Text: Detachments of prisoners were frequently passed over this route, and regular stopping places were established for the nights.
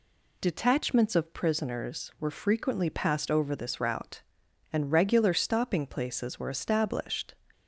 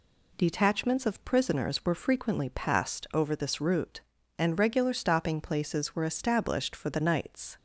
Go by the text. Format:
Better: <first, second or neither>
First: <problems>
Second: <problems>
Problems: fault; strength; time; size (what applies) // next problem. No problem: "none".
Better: second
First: stops before "for the nights"; at 7.5 s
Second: none